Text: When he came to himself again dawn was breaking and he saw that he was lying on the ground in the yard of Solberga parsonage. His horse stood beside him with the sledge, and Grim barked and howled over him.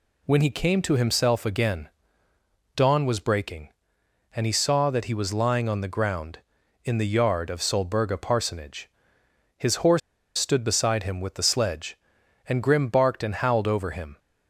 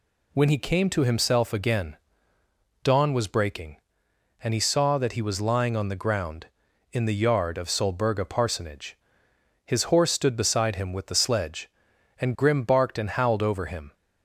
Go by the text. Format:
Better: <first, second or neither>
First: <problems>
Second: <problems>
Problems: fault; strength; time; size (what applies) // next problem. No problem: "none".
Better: second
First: pauses between "again" and "dawn"; noticeable; at 1.8 s; 0.88 s long // pauses between "horse" and "stood"; at 10.0 s; 0.38 s long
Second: pauses between "again" and "dawn"; noticeable; at 1.9 s; 0.88 s long